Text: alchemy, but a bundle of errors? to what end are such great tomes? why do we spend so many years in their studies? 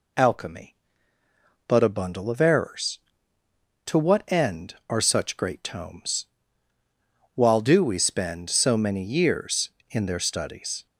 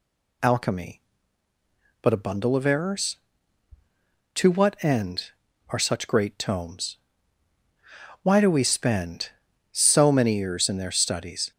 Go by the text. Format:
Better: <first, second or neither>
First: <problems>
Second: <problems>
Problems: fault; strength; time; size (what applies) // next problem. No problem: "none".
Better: second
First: says "while" for "why"; at 7.3 s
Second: none